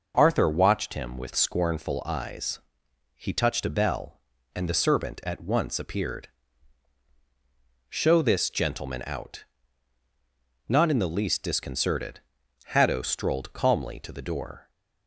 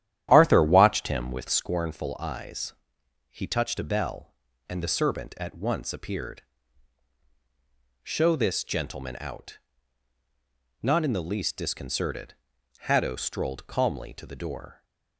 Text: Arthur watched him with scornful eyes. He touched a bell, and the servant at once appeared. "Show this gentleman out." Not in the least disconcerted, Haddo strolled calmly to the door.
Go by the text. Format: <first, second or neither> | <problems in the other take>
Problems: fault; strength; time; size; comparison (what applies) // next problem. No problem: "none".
first | starts louder than the rest; strong; until 1.6 s; 11 dB